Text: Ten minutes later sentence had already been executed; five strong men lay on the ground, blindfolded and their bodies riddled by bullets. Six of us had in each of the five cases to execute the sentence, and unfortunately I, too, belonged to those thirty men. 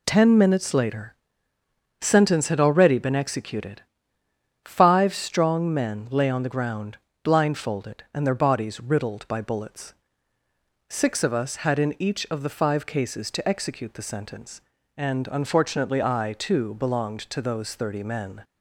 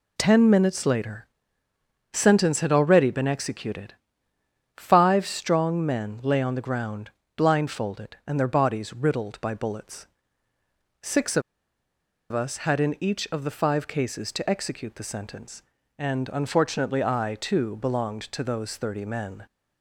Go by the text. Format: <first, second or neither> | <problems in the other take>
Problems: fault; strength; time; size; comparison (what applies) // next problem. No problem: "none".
first | pauses between "later" and "sentence"; noticeable; at 1.2 s; 0.86 s long; noticeable in the first // pauses between "of" and "us"; noticeable; at 11.4 s; 0.90 s long